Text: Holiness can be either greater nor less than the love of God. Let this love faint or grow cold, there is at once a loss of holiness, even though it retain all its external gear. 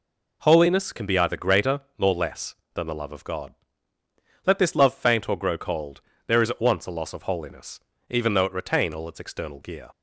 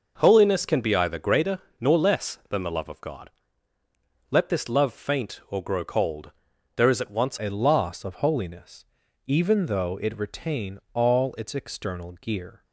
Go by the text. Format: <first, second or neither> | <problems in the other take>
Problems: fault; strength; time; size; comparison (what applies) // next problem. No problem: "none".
first | pauses between "greater" and "nor"; slight; at 1.5 s; 0.20 s long; slight in the first // changes voice at "a"; from 7.3 s on; 5.3 s long